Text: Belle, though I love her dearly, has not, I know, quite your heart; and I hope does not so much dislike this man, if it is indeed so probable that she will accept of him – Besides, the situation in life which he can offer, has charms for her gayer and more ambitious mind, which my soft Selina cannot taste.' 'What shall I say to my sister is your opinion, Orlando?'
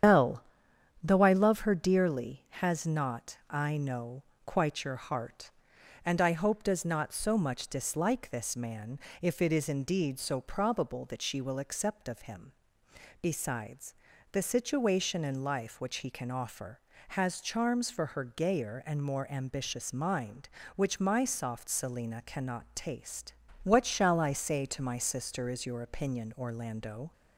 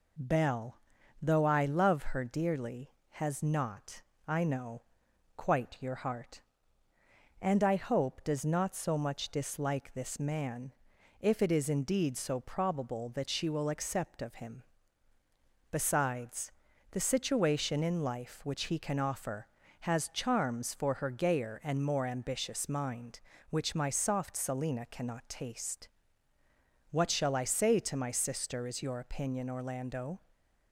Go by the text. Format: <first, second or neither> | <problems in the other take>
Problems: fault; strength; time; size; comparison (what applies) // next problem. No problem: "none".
second | loses the start of "Belle"; at 0.0 s; 85 ms // starts louder than the rest; strong; until 1.6 s; 8.5 dB